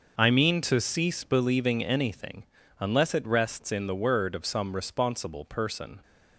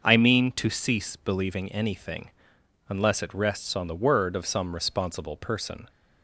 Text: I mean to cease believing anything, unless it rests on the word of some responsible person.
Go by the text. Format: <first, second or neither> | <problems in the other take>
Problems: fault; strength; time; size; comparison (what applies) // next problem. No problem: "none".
second | starts louder than the rest; noticeable; until 1.1 s; 6 dB; also in the second // says "in" for "on"; at 3.7 s